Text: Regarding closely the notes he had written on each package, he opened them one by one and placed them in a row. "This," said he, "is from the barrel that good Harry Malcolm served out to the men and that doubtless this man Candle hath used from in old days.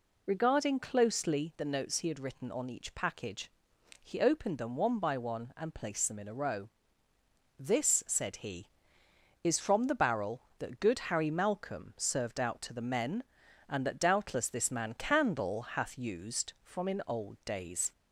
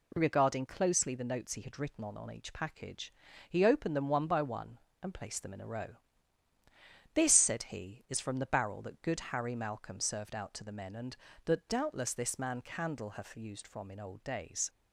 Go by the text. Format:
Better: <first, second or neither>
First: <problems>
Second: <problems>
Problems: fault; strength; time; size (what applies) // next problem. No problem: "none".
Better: first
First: none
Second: says "on" twice; at 2.1 s